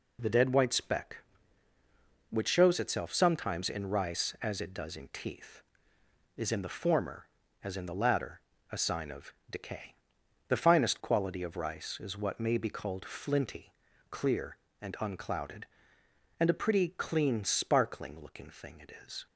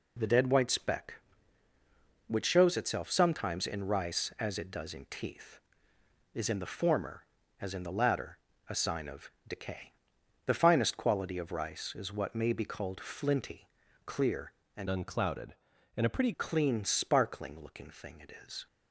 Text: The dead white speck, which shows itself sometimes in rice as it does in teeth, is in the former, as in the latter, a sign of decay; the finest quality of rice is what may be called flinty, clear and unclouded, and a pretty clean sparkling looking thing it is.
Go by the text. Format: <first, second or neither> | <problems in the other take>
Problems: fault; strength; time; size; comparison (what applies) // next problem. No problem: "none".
first | pauses between "of" and "decay"; slight; at 9.2 s; 0.18 s long; slight in the first // changes voice from "unclouded" to "pretty"; from 14.8 to 16.3 s; 1.5 s long